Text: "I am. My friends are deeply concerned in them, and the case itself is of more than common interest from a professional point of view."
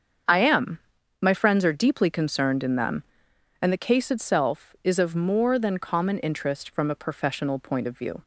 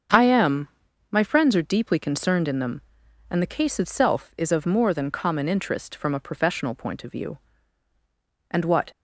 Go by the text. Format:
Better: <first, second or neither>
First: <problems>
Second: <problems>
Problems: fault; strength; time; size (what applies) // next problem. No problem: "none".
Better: first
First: starts louder than the rest; strong; until 1.6 s; 7 dB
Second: starts louder than the rest; until 1.5 s; 7 dB // goes on to say "And what"; slight; from 8.5 s on; 0.40 s long